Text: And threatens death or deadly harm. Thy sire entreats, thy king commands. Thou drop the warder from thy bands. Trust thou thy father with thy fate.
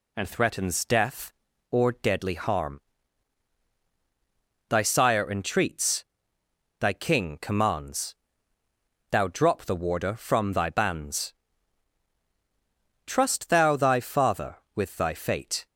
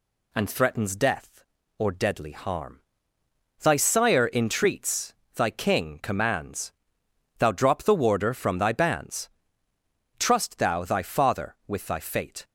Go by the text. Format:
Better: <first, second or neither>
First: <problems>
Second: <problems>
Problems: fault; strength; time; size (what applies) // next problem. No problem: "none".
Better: neither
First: none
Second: none